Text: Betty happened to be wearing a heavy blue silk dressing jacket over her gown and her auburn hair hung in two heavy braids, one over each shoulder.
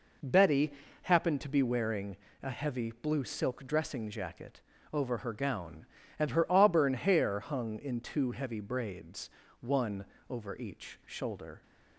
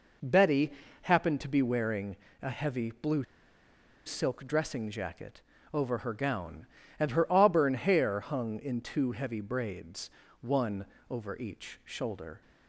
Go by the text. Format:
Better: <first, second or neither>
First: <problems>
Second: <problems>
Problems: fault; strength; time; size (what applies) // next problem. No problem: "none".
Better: first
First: pauses between "Betty" and "happened"; slight; at 0.7 s; 0.30 s long // pauses between "wearing" and "a"; slight; at 2.1 s; 0.26 s long // pauses between "jacket" and "over"; slight; at 4.6 s; 0.32 s long // pauses between "one" and "over"; slight; at 10.0 s; 0.24 s long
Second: pauses between "Betty" and "happened"; slight; at 0.7 s; 0.30 s long // pauses between "wearing" and "a"; slight; at 2.1 s; 0.26 s long // pauses between "blue" and "silk"; noticeable; at 3.2 s; 0.83 s long // pauses between "jacket" and "over"; slight; at 5.4 s; 0.32 s long // pauses between "one" and "over"; slight; at 10.8 s; 0.24 s long